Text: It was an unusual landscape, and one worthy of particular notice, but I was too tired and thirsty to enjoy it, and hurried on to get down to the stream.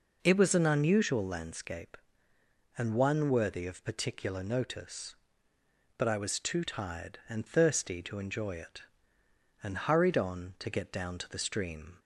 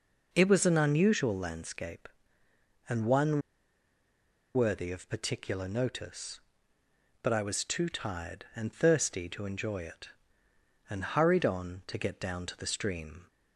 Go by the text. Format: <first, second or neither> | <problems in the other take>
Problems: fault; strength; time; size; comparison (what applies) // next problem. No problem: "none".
first | pauses between "one" and "worthy"; at 3.4 s; 1.1 s long